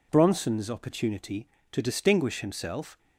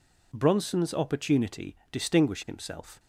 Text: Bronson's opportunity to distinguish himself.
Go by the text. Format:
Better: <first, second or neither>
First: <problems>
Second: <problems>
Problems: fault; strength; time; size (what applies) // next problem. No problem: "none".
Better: first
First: none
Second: skips "to"; at 1.8 s